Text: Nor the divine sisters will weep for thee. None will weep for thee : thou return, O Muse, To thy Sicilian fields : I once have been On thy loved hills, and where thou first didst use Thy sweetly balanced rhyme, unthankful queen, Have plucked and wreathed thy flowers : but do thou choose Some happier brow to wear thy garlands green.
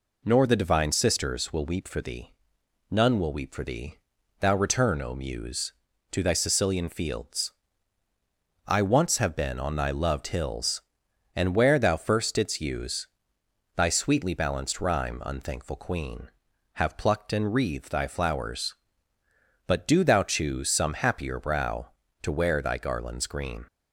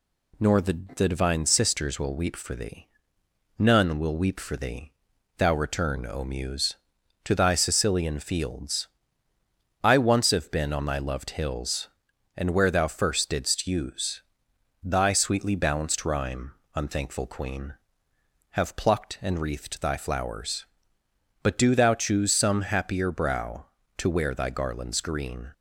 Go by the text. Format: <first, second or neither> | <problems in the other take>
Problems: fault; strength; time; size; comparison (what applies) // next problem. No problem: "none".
first | says "the" twice; at 0.9 s // pauses between "use" and "Thy"; noticeable; at 14.2 s; 0.60 s long; noticeable in the first